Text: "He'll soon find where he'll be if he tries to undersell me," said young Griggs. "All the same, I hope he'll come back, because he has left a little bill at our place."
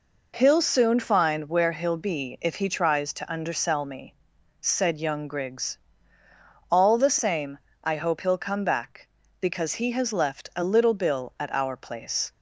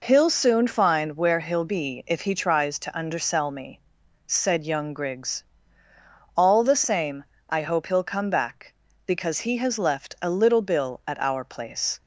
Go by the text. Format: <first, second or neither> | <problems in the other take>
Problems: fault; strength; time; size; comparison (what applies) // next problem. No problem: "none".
neither | none